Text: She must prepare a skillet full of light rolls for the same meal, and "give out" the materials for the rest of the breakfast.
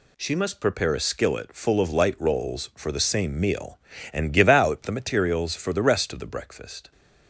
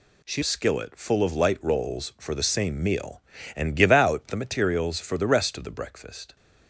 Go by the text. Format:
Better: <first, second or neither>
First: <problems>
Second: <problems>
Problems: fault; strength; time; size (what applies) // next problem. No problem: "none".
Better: first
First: none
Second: skips "must prepare a"; at 0.4 s